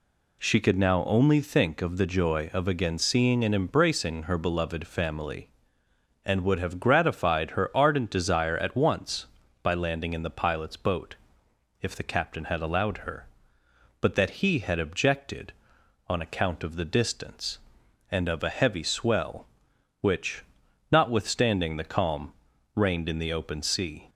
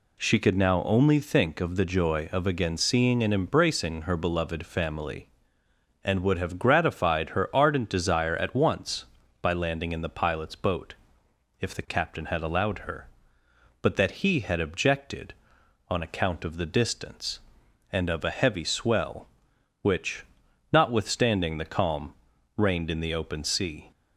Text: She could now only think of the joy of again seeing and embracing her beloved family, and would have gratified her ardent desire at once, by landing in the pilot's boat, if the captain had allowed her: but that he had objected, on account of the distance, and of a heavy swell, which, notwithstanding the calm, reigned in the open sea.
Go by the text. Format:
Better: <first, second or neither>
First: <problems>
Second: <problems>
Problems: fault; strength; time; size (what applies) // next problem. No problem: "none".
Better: neither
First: none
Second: none